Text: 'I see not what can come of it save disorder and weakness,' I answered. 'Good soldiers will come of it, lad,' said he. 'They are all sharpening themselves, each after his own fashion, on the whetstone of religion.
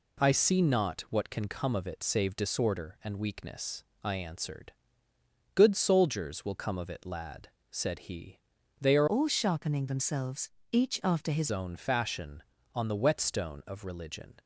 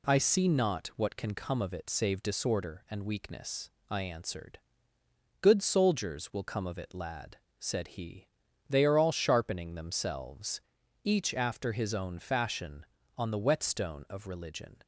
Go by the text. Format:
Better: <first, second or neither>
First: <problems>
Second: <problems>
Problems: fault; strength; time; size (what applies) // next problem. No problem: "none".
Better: second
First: changes voice from "all" to "his"; from 9.0 to 11.4 s; 2.4 s long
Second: none